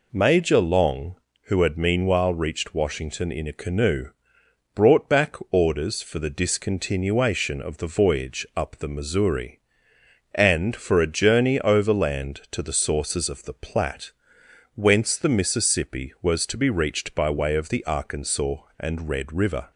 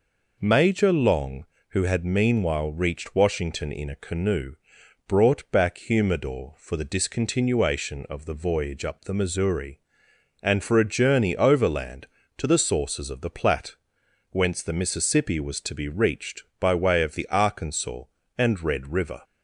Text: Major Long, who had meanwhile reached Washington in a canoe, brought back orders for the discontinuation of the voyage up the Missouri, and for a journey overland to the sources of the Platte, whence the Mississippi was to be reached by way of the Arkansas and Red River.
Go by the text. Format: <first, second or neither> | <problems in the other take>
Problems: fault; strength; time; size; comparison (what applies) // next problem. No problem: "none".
first | says "humidor" for "orders"; at 5.7 s